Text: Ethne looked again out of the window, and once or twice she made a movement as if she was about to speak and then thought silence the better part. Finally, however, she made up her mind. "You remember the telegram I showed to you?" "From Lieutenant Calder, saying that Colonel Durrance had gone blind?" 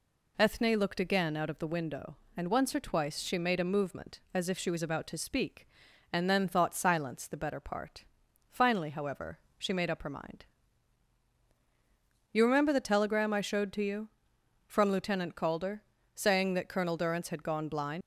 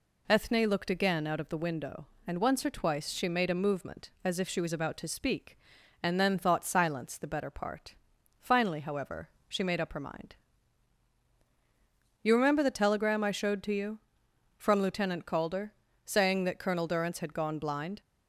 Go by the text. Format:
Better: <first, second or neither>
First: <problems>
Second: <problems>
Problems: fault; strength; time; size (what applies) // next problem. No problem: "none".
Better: second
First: leaves "blind" unfinished; at 18.0 s; 90 ms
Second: none